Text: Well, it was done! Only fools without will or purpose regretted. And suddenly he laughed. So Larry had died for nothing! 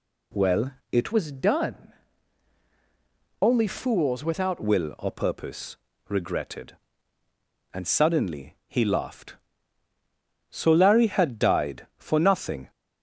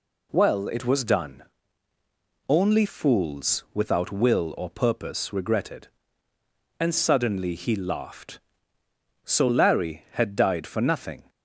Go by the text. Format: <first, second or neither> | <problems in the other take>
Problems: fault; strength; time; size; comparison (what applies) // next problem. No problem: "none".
second | changes voice from "was" to "without"; from 1.1 to 4.6 s; 3.5 s long // pauses between "purpose" and "regretted"; slight; at 5.7 s; 0.32 s long